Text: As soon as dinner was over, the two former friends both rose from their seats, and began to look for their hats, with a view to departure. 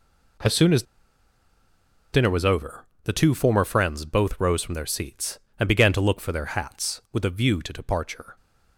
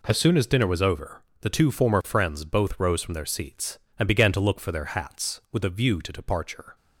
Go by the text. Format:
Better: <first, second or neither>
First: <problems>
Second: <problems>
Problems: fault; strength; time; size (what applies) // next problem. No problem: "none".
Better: second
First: pauses between "as" and "dinner"; strong; at 0.8 s; 1.3 s long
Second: none